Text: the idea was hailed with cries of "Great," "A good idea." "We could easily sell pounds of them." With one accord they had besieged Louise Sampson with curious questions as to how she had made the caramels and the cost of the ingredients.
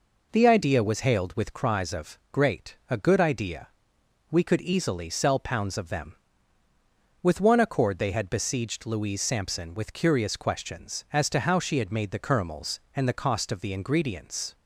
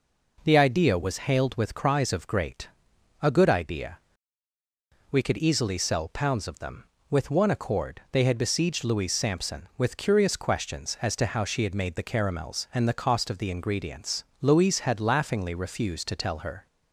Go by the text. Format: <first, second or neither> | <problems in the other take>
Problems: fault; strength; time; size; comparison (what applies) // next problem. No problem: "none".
first | goes on to say "Louise had laughingly refused to tell her"; strong; from 14.4 s on; 2.2 s long